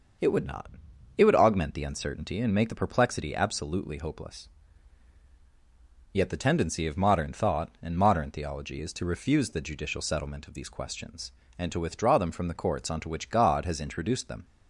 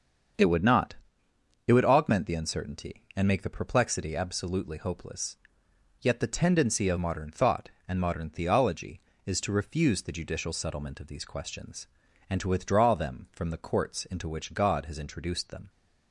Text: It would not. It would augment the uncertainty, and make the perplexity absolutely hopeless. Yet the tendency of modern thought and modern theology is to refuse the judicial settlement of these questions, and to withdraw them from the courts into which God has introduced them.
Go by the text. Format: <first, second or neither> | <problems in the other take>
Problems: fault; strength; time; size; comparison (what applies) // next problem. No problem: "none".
second | starts louder than the rest; until 1.6 s; 6 dB; strong in the second // says "onto" for "into"; at 12.9 s